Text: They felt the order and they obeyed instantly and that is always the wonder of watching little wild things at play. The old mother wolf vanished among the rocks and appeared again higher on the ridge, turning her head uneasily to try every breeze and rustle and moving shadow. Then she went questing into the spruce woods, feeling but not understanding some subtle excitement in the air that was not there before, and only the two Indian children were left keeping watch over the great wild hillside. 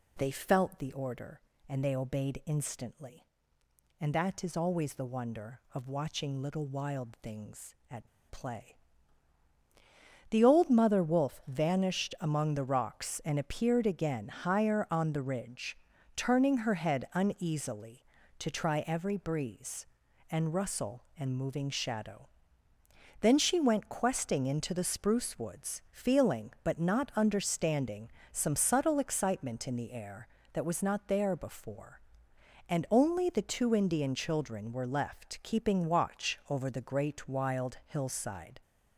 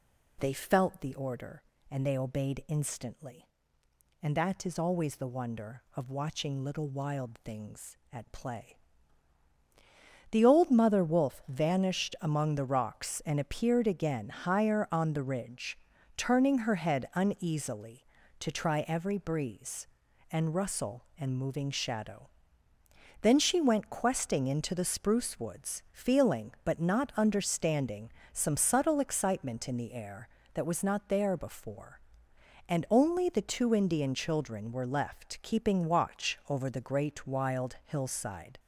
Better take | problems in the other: second | pauses between "at" and "play"; slight; at 8.0 s; 0.24 s long // pauses between "understanding" and "some"; slight; at 28.1 s; 0.22 s long; slight in the second

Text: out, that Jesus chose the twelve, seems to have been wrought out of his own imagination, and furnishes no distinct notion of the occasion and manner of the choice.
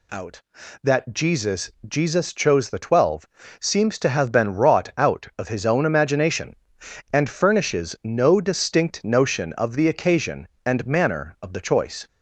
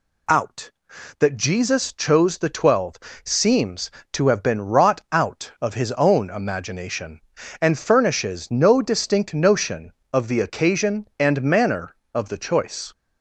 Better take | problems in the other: second | says "Jesus" twice; at 1.8 s

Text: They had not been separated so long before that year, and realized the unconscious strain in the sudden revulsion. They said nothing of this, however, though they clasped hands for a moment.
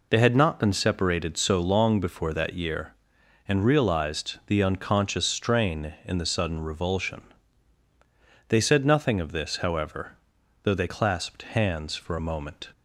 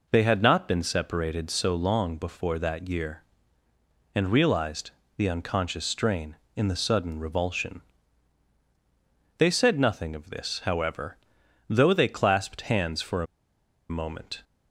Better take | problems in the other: first | pauses between "realized" and "the"; slight; at 4.9 s; 0.26 s long // pauses between "a" and "moment"; noticeable; at 13.2 s; 0.65 s long

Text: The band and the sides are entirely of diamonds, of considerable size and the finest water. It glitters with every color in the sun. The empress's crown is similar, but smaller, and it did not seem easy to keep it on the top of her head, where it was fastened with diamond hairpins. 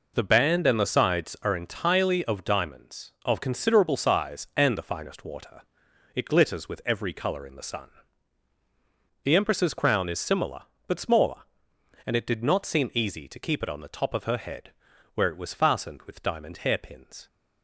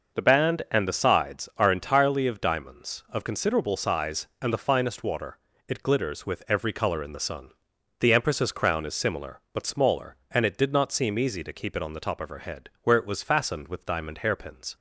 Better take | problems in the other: neither | none

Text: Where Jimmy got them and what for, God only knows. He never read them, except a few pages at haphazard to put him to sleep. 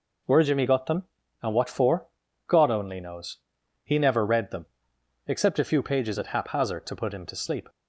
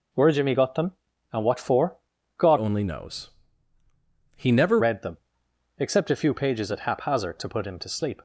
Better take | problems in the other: first | changes voice from "only" to "never"; from 2.5 to 4.7 s; 2.2 s long

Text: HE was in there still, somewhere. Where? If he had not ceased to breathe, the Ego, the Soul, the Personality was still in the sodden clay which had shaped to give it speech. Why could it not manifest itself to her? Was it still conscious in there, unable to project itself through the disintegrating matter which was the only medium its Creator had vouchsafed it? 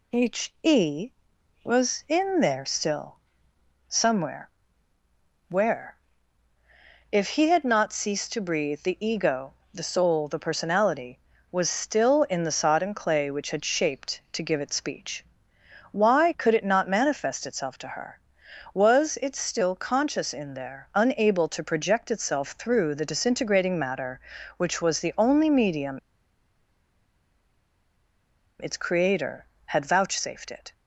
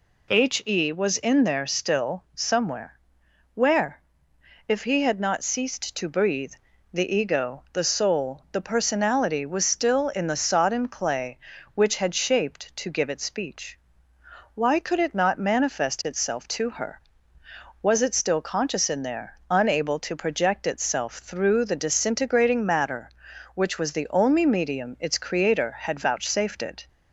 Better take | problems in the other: second | pauses between "medium" and "its"; strong; at 25.9 s; 2.6 s long

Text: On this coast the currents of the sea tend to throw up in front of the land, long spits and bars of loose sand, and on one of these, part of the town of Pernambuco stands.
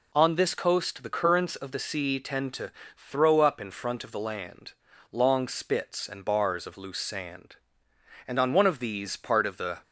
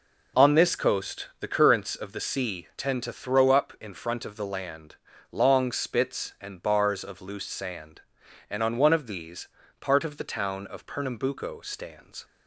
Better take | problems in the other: second | pauses between "to" and "throw"; slight; at 2.7 s; 0.24 s long // stops before "town of Pernambuco stands"; at 9.8 s

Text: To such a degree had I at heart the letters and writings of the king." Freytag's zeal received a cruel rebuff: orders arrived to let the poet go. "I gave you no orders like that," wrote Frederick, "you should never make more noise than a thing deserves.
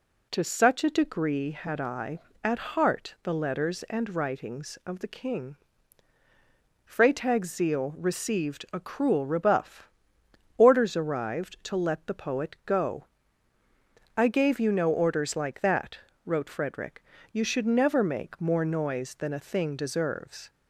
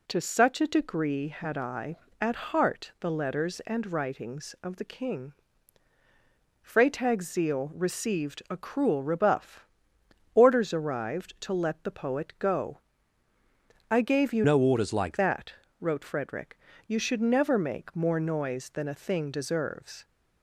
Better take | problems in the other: first | changes voice from "no" to "like"; from 14.4 to 15.1 s; 0.7 s long

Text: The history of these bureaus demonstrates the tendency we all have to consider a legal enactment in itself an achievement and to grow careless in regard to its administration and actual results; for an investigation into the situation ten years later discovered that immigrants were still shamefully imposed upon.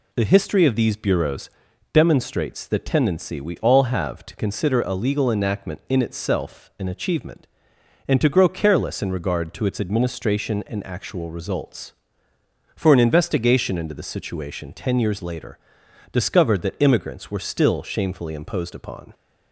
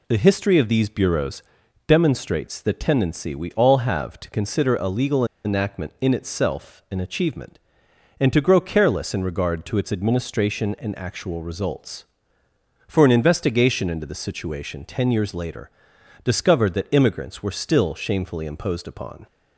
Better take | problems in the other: first | pauses between "bureaus" and "demonstrates"; noticeable; at 1.4 s; 0.46 s long; also in the first // pauses between "legal" and "enactment"; slight; at 5.2 s; 0.20 s long // pauses between "later" and "discovered"; noticeable; at 15.7 s; 0.50 s long; noticeable in the first

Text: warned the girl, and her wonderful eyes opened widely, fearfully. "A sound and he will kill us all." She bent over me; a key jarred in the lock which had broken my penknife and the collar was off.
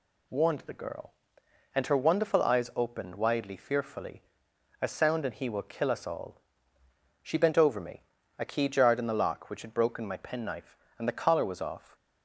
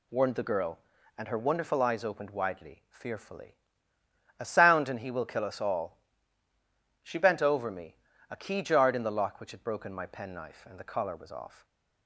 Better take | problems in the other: neither | none

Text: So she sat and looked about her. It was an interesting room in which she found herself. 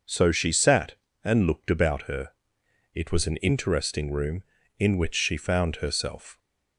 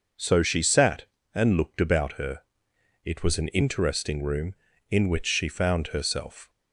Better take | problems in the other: neither | none

